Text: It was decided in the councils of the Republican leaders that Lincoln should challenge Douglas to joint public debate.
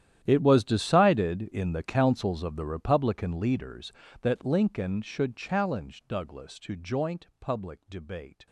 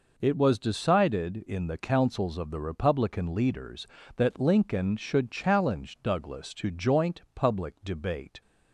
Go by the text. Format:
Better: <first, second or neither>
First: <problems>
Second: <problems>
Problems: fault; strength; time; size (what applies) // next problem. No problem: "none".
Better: second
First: gets quieter; strong; throughout; 17.5 dB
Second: none